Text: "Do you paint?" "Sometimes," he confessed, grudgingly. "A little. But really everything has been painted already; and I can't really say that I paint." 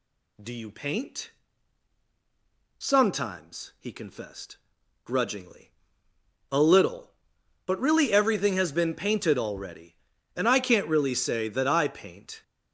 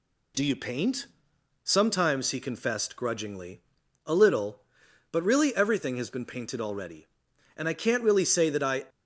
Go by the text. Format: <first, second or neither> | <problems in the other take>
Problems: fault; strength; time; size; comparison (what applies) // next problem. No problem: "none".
first | stops before "paint"; at 8.8 s